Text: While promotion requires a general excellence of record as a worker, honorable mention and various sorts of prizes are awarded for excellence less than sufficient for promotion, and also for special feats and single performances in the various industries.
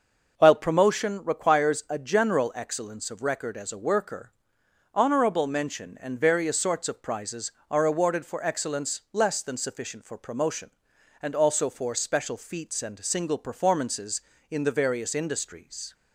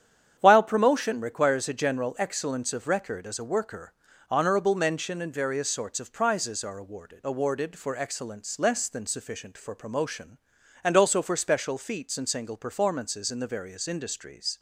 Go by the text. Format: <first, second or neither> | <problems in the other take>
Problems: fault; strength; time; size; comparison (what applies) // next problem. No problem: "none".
first | starts louder than the rest; strong; until 1.4 s; 9 dB // says "awarded" twice; at 7.2 s